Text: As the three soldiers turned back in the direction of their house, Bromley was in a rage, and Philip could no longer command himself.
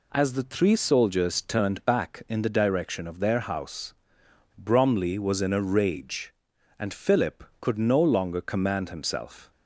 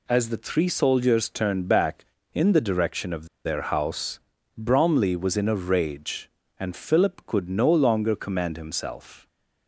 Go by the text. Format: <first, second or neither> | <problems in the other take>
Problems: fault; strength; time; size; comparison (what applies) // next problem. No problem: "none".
first | pauses between "of" and "their"; slight; at 3.2 s; 0.19 s long